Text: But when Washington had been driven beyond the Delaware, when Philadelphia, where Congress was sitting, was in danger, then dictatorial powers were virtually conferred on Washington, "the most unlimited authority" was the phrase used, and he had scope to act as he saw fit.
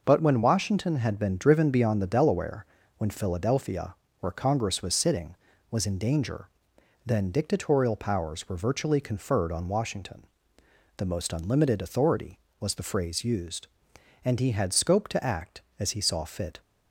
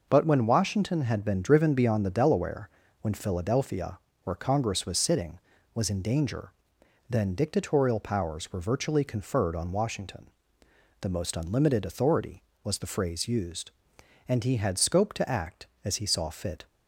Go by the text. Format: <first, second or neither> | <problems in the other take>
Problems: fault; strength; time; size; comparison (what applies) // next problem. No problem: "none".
neither | none